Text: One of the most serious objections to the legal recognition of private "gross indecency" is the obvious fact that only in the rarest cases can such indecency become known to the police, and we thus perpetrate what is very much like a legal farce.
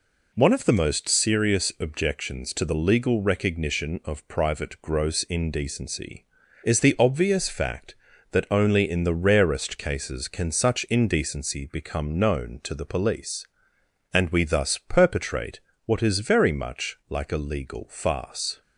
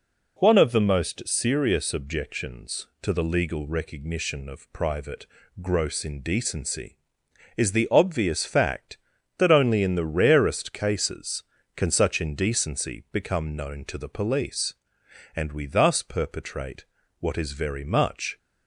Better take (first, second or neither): first